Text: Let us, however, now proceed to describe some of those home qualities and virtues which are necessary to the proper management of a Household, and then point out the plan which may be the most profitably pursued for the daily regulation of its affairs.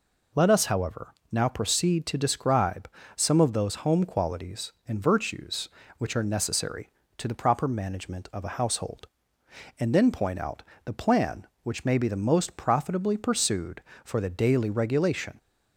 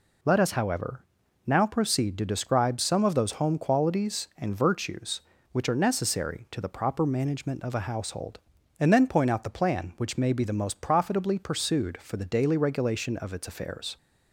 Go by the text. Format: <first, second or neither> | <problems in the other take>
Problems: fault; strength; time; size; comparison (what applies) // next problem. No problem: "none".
second | pauses between "describe" and "some"; slight; at 2.8 s; 0.26 s long // pauses between "out" and "the"; slight; at 10.6 s; 0.22 s long // stops before "of its affairs"; at 15.3 s